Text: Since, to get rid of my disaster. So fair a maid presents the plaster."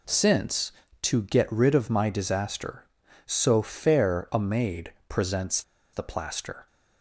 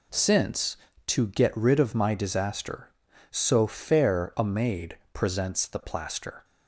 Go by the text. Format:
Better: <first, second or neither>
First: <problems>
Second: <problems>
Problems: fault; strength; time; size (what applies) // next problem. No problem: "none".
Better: second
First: pauses between "maid" and "presents"; slight; at 4.9 s; 0.16 s long // pauses between "presents" and "the"; slight; at 5.6 s; 0.31 s long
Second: pauses between "maid" and "presents"; slight; at 4.9 s; 0.16 s long